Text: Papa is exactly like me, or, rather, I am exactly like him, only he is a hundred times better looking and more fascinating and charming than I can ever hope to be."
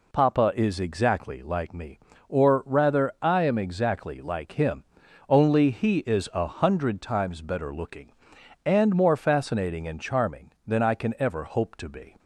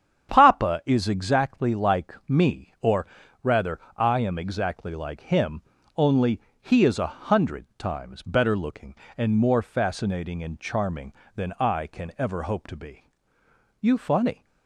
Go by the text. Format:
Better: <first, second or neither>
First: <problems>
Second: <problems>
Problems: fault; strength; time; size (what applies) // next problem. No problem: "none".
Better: first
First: none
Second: starts louder than the rest; strong; until 1.3 s; 9 dB // pauses between "only" and "he"; slight; at 6.3 s; 0.22 s long // goes on to say "You funny"; noticeable; from 13.8 s on; 0.64 s long